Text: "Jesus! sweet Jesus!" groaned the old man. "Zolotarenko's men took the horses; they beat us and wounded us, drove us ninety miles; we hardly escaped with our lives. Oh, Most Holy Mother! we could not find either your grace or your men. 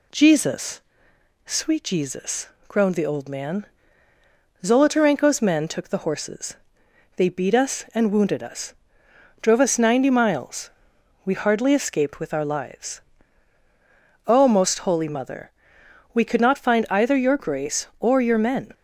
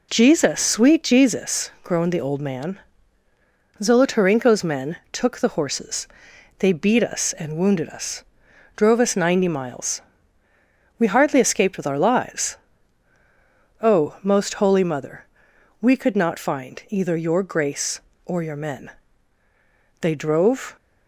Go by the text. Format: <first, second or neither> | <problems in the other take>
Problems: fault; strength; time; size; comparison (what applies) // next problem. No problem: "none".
first | pauses between "men" and "took"; slight; at 4.9 s; 0.16 s long // goes on to say "They drove"; noticeable; from 19.9 s on; 0.76 s long